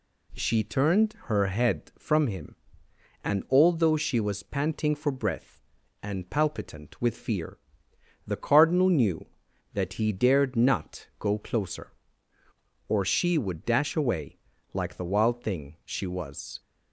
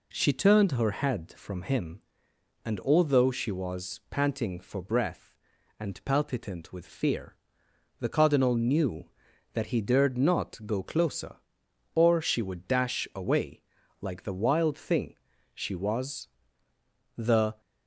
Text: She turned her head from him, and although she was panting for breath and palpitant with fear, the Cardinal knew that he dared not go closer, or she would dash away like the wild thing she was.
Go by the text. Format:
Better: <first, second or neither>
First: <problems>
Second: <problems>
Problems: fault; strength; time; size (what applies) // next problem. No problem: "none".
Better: first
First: pauses between "away" and "like"; slight; at 14.3 s; 0.34 s long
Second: pauses between "away" and "like"; at 13.6 s; 0.38 s long // pauses between "thing" and "she"; at 15.1 s; 0.40 s long // goes on to say "The"; slight; from 17.1 s on; 0.44 s long